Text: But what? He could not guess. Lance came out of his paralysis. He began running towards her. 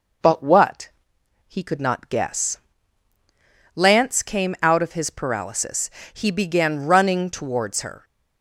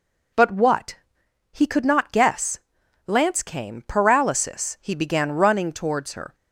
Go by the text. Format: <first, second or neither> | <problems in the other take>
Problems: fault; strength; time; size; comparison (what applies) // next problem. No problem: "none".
first | skips "out of his"; at 3.8 s